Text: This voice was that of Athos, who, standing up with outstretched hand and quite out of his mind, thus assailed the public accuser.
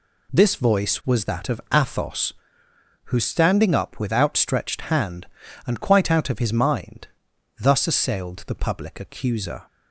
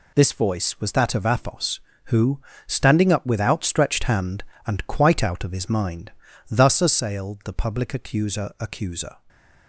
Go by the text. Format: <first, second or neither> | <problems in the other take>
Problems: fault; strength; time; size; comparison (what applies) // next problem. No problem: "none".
first | says "accuser" twice; at 8.5 s